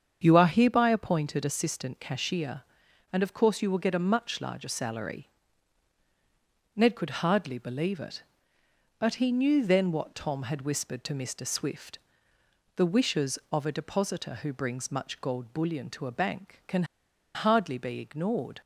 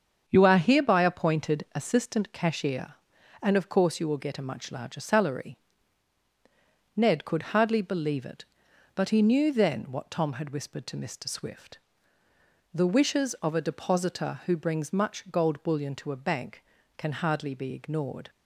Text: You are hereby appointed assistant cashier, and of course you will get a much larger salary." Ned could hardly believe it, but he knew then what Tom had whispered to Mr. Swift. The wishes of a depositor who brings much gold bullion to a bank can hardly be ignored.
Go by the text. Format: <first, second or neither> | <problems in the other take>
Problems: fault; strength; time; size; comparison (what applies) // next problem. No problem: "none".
second | starts louder than the rest; strong; until 1.2 s; 7.5 dB; strong in the second // pauses between "can" and "hardly"; noticeable; at 16.8 s; 0.50 s long